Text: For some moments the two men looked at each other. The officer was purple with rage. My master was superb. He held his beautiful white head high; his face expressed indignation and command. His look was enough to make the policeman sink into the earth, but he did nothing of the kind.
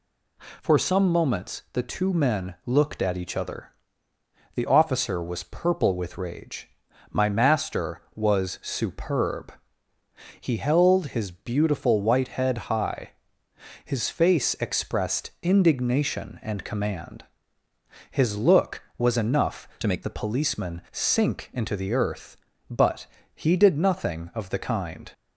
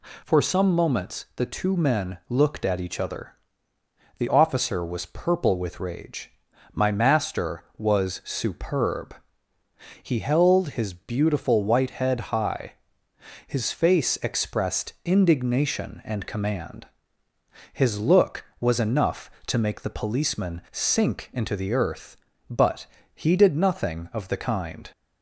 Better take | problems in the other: second | changes voice from "to" to "make"; from 19.8 to 20.0 s; 0.2 s long // pauses between "but" and "he"; slight; at 23.0 s; 0.28 s long; slight in the second

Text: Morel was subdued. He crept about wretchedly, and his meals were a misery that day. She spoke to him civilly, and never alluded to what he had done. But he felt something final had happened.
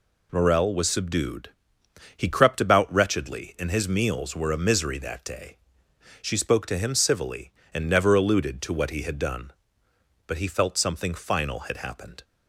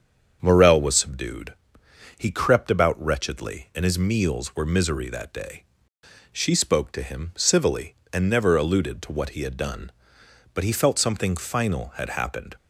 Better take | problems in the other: first | starts louder than the rest; strong; until 1.4 s; 7 dB // skips "a"; at 4.6 s

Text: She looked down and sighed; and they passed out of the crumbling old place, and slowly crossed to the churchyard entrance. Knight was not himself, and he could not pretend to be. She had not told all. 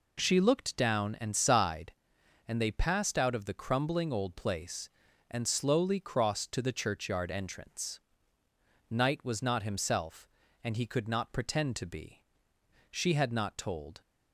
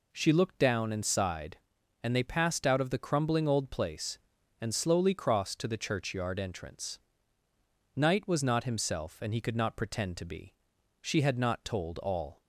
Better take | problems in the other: second | stops before "all"; at 14.0 s

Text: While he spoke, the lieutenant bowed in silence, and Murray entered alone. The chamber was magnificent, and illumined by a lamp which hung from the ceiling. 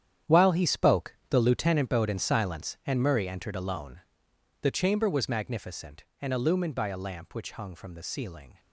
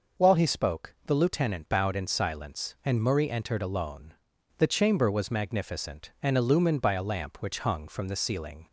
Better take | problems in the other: second | gets quieter; strong; throughout; 12 dB

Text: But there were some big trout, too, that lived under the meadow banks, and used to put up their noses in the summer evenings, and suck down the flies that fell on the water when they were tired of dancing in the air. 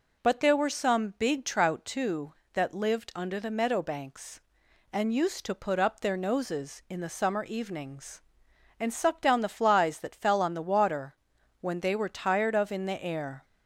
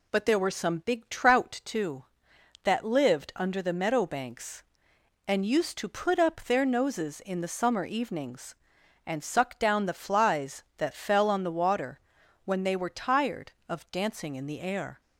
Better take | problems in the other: second | pauses between "water" and "when"; noticeable; at 11.1 s; 0.46 s long; noticeable in the second // skips "dancing"; at 12.7 s

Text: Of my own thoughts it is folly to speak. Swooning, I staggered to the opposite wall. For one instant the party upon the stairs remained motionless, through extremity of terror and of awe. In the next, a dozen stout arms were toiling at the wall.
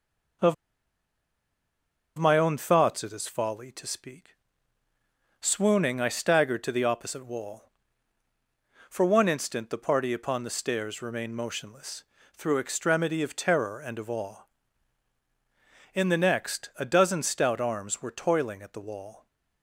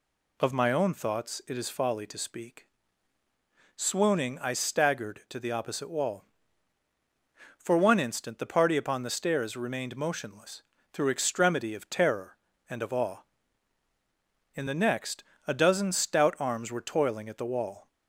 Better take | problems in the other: second | pauses between "Of" and "my"; strong; at 0.5 s; 1.6 s long

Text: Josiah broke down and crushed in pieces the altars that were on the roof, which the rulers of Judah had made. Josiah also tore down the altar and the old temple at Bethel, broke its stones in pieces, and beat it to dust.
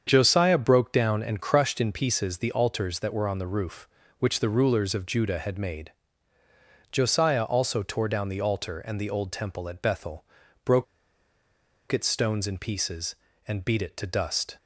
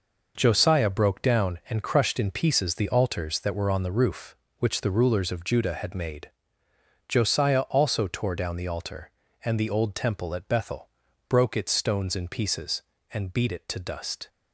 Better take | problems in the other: second | starts louder than the rest; strong; until 1.0 s; 7 dB // pauses between "broke" and "its"; at 10.8 s; 1.0 s long

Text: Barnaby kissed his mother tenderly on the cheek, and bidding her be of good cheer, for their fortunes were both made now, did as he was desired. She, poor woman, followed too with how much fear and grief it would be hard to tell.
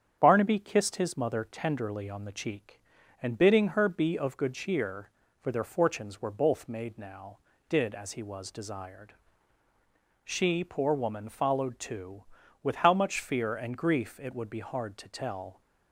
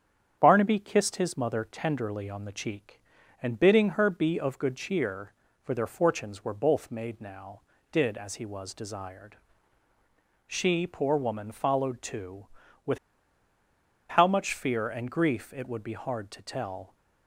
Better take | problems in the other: first | starts louder than the rest; strong; until 1.3 s; 8.5 dB; strong in the first // pauses between "with" and "how"; at 12.9 s; 1.1 s long

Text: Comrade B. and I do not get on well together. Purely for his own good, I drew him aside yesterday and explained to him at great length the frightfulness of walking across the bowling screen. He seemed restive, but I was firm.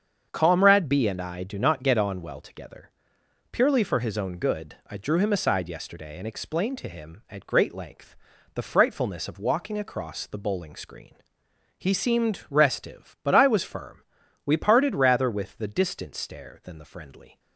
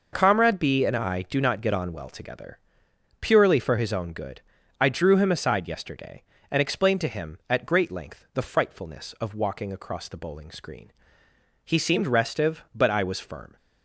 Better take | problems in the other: second | starts louder than the rest; until 1.3 s; 7 dB // pauses between "length" and "the"; at 8.1 s; 0.38 s long // goes on to say "We parted rather with the Distant Stare than the Friendly"; strong; from 14.4 s on; 2.9 s long

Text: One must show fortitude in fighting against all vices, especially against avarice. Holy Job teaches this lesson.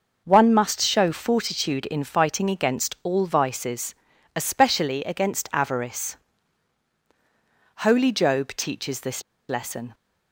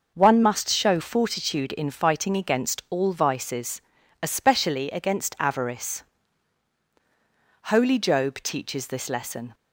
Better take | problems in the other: second | pauses between "this" and "lesson"; slight; at 9.2 s; 0.27 s long

